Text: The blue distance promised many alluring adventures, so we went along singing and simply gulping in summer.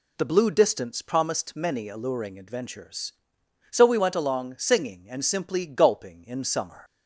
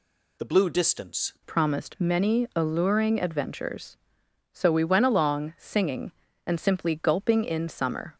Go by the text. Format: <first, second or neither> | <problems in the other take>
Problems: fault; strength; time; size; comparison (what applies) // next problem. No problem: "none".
first | changes voice at "promised"; from 1.4 s on; 6.7 s long